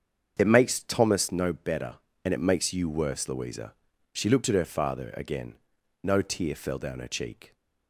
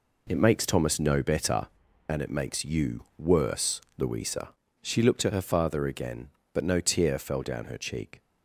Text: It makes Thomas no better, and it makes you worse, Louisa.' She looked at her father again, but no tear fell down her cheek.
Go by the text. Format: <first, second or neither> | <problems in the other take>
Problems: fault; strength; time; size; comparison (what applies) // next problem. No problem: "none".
second | starts louder than the rest; until 1.3 s; 7 dB // skips "but"; at 5.7 s